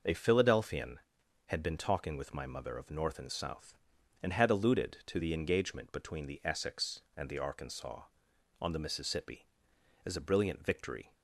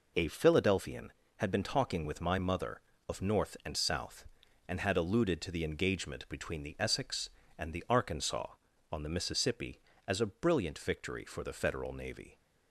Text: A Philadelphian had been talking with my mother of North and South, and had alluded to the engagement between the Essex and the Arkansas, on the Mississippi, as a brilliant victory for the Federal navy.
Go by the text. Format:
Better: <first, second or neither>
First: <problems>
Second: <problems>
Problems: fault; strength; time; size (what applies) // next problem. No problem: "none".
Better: second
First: stops before "for the Federal navy"; at 11.1 s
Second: none